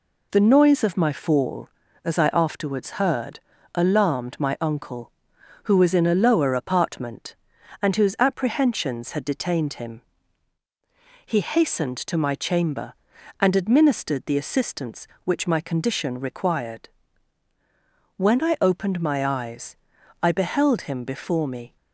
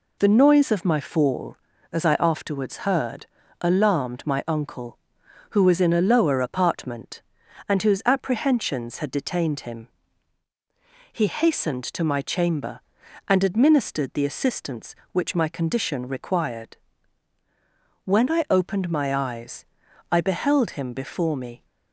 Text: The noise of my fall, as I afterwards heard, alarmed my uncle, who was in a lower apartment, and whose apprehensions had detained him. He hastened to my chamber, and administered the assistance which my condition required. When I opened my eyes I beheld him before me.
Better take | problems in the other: neither | pauses between "eyes" and "I"; noticeable; the same in both

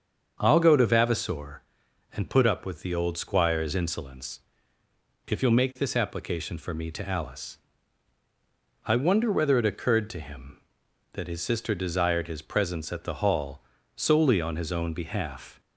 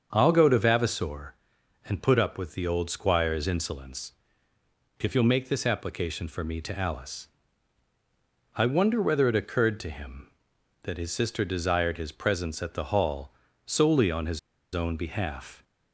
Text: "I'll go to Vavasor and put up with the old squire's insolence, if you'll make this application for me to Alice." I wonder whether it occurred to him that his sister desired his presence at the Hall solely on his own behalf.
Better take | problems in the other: first | starts louder than the rest; until 1.1 s; 7 dB; also in the first // pauses between "Hall" and "solely"; slight; at 13.3 s; 0.34 s long; slight in the first // pauses between "his" and "own"; slight; at 14.3 s; 0.35 s long

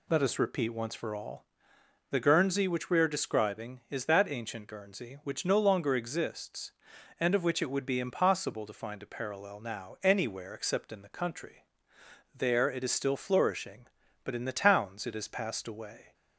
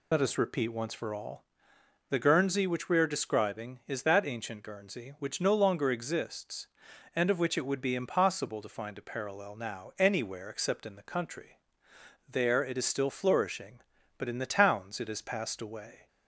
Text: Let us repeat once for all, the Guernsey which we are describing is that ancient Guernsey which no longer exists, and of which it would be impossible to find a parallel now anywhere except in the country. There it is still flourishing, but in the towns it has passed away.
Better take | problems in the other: first | loses the start of "Let"; at 0.1 s; 30 ms

